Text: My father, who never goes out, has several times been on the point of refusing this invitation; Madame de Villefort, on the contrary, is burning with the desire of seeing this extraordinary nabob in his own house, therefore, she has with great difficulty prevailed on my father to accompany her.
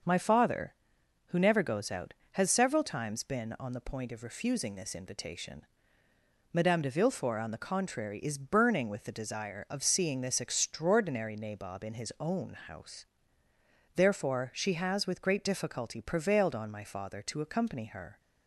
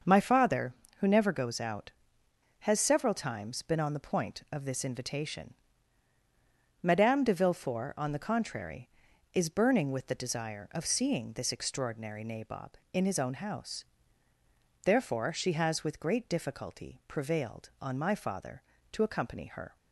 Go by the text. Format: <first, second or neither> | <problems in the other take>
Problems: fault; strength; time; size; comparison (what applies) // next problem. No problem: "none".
first | starts louder than the rest; until 1.2 s; 6.5 dB; also in the first // skips "refusing"; at 4.6 s